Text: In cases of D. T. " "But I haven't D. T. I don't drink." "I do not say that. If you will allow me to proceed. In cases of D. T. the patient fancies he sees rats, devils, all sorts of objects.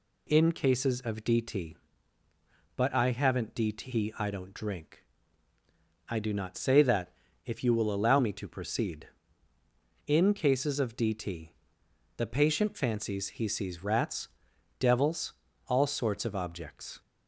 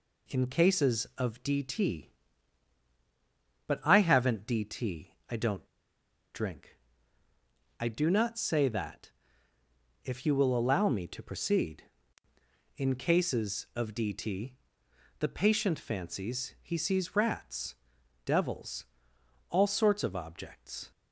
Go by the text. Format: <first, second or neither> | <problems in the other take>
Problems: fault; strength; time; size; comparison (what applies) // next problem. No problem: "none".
first | pauses between "T" and "I"; slight; at 5.1 s; 0.16 s long // pauses between "don't" and "drink"; noticeable; at 5.6 s; 0.68 s long // pauses between "T" and "the"; noticeable; at 14.5 s; 0.60 s long; noticeable in the first